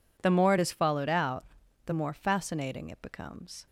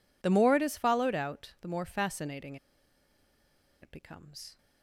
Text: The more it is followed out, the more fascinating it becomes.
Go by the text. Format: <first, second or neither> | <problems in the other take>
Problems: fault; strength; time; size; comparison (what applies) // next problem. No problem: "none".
first | pauses between "fascinating" and "it"; strong; at 2.5 s; 1.2 s long